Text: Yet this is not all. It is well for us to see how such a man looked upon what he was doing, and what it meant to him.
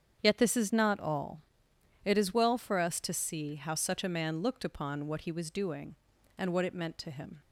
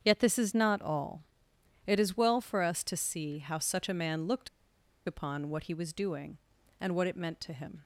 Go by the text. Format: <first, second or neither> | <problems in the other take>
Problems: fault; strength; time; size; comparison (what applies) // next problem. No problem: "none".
first | starts louder than the rest; strong; until 1.0 s; 8 dB; strong in the first // pauses between "looked" and "upon"; noticeable; at 4.4 s; 0.58 s long